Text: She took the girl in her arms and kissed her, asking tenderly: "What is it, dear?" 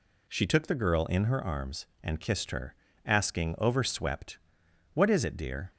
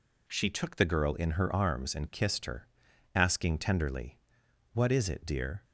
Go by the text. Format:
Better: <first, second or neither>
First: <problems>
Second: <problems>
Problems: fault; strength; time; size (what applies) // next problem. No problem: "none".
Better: second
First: says "overswept" for "tenderly"; at 3.5 s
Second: none